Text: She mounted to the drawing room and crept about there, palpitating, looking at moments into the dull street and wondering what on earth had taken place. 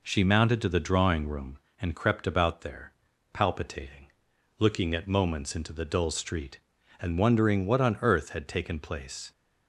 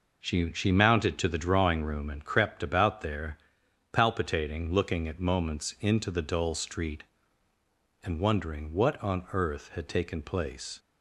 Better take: first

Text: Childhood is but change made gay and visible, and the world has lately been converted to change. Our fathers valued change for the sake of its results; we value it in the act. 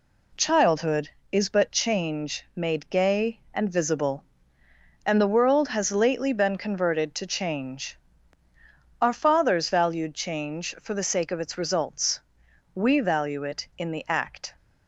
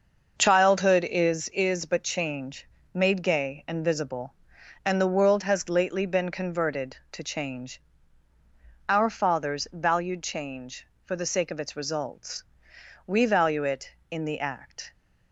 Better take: first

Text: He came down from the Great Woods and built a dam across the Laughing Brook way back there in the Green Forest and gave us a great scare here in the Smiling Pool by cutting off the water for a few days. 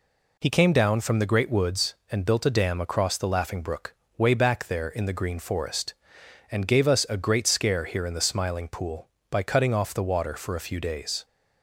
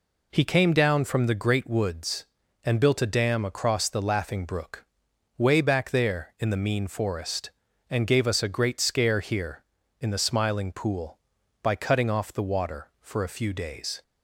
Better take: first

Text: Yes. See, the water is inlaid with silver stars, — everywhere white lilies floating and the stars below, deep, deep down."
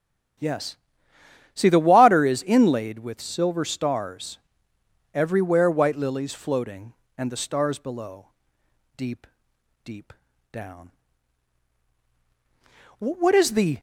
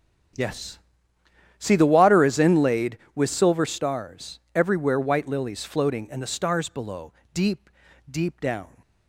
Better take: second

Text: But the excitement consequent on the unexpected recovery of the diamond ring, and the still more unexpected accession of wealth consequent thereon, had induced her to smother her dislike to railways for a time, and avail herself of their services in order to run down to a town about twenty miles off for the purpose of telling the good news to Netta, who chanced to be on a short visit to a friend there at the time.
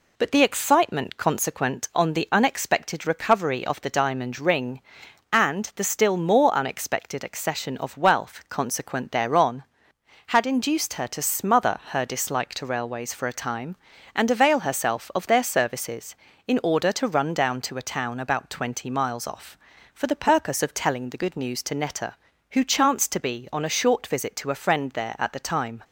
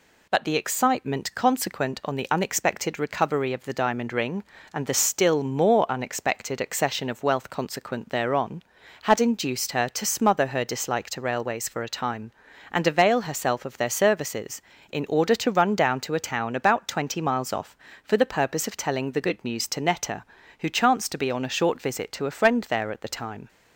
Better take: neither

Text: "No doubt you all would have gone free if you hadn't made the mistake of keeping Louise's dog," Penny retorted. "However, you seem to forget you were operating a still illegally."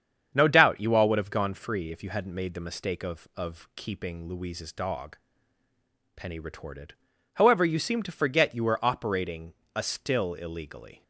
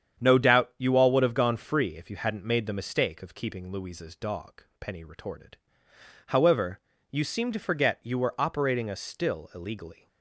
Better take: second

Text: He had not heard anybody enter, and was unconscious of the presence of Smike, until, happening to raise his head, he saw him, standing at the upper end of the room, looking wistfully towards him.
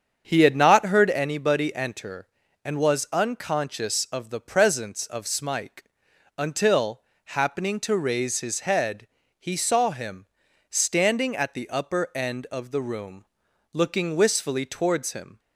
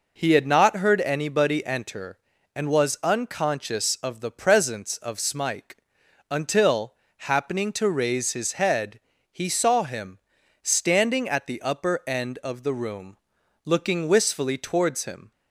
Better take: second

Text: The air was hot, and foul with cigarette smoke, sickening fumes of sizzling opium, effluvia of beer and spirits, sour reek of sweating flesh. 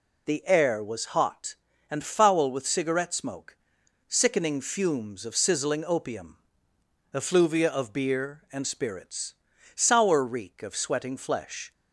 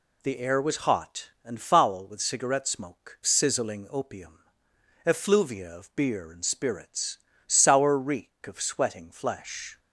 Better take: first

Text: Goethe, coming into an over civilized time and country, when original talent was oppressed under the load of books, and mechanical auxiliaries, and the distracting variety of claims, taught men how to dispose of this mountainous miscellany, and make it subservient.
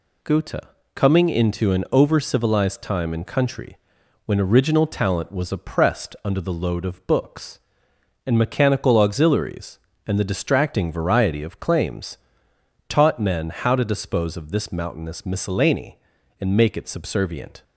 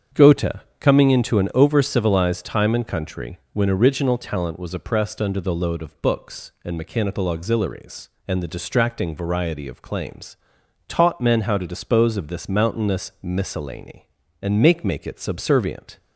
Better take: first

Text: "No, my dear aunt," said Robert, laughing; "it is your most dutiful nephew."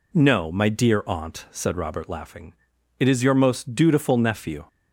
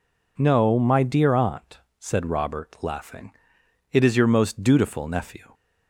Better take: neither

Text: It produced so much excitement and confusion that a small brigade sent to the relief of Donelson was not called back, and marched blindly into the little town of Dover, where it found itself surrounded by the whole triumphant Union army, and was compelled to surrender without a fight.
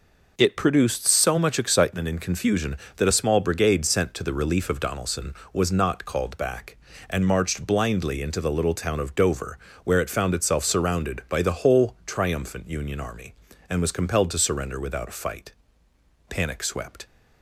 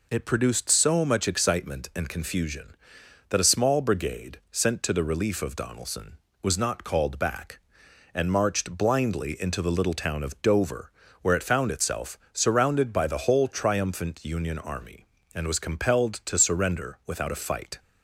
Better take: second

